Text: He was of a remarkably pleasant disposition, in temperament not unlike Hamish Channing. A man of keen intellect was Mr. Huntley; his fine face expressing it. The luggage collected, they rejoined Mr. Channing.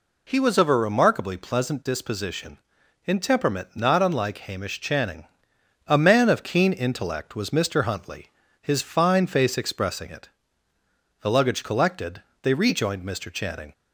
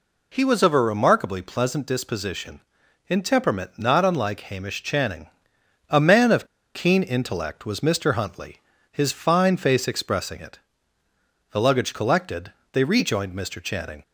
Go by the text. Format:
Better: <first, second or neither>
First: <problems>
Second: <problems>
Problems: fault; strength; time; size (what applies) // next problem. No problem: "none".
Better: first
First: none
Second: pauses between "of" and "keen"; slight; at 6.4 s; 0.28 s long